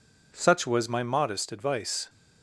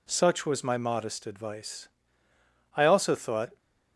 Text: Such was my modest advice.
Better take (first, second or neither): first